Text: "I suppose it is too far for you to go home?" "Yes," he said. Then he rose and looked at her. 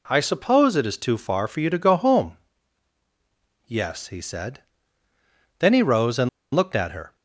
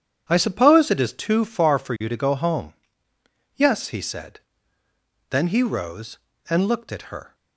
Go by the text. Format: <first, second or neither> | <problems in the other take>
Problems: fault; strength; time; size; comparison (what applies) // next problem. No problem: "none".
second | pauses between "and" and "looked"; slight; at 6.2 s; 0.26 s long